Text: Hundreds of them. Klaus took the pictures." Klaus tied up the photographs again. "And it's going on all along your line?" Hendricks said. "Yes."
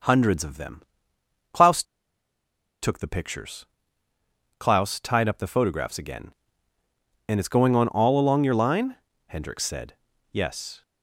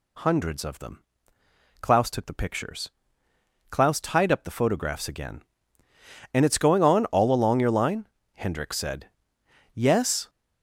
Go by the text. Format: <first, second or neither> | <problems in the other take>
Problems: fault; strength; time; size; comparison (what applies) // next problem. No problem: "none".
second | starts louder than the rest; noticeable; until 1.7 s; 6 dB // pauses between "Klaus" and "took"; at 1.8 s; 0.99 s long